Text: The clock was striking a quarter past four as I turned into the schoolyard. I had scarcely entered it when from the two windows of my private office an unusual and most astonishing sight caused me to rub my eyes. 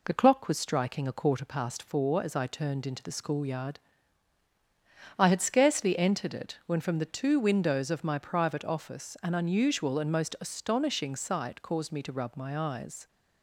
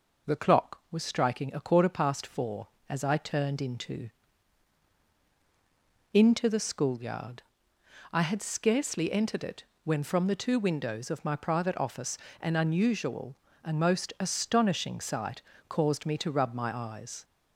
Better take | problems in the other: first | says "into" twice; at 6.1 s // pauses between "it" and "when"; slight; at 9.6 s; 0.18 s long // pauses between "office" and "an"; slight; at 12.1 s; 0.24 s long // pauses between "sight" and "caused"; slight; at 15.3 s; 0.28 s long

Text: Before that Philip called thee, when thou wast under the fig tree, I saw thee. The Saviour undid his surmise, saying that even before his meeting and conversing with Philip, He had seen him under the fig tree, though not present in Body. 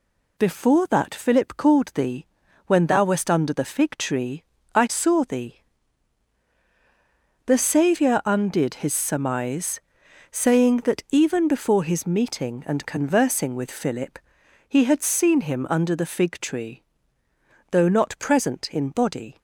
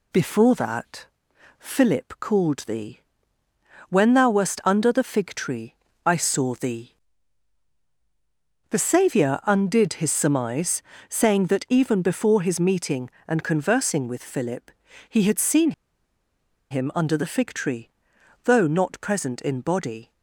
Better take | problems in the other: first | pauses between "that" and "Philip"; noticeable; at 1.0 s; 0.50 s long // pauses between "seen" and "him"; at 15.7 s; 0.99 s long

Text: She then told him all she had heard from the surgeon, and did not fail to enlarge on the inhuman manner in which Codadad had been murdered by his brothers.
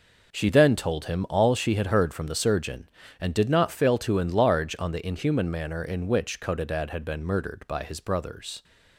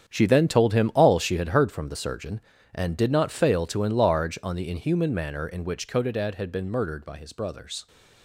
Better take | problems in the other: first | gets quieter; strong; throughout; 12 dB

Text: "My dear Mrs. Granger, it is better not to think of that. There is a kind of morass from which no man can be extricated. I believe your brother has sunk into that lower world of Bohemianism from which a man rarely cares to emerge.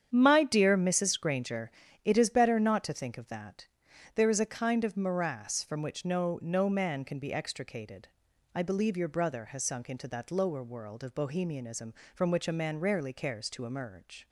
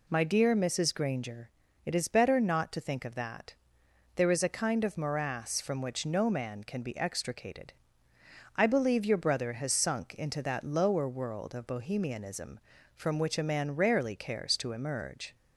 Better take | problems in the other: second | starts louder than the rest; strong; until 1.1 s; 8.5 dB // says "no" twice; at 6.4 s

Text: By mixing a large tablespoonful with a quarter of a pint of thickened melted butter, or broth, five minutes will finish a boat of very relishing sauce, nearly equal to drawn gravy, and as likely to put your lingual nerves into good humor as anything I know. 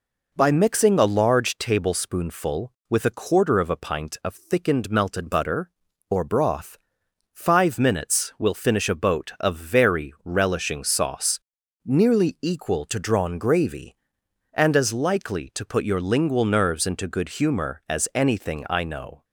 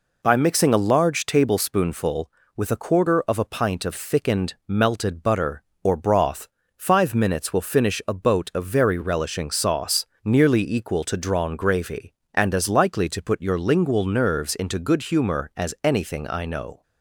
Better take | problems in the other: neither | none

